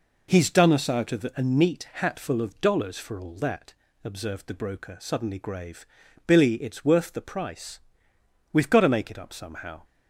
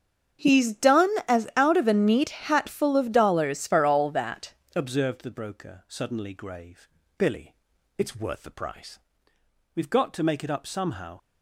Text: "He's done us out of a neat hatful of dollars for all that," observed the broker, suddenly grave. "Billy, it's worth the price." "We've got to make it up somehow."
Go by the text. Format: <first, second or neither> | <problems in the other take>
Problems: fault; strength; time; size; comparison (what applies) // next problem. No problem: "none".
first | starts louder than the rest; strong; until 1.7 s; 8.5 dB // says "as" for "us"; at 1.2 s